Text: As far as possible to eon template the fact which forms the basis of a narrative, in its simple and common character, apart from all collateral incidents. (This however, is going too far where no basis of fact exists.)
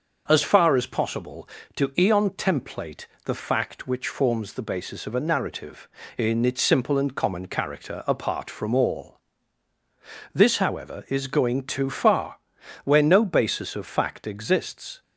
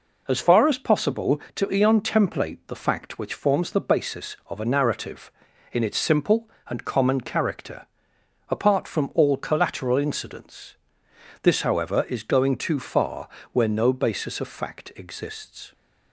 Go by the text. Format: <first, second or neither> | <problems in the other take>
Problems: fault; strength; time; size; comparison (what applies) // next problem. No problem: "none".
second | starts louder than the rest; until 1.2 s; 6 dB // pauses between "template" and "the"; slight; at 3.0 s; 0.20 s long // skips "collateral incidents"; at 9.7 s // pauses between "far" and "where"; noticeable; at 12.3 s; 0.46 s long; slight in the second